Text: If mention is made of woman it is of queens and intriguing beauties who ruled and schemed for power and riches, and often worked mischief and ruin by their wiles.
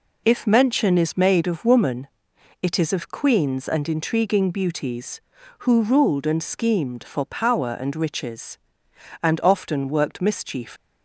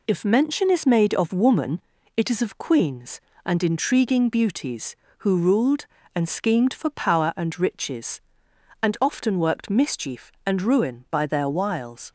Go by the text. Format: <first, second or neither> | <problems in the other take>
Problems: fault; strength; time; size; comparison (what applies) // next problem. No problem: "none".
second | pauses between "woman" and "it"; noticeable; at 2.0 s; 0.54 s long; slight in the second // stops before "and ruin by their wiles"; at 10.7 s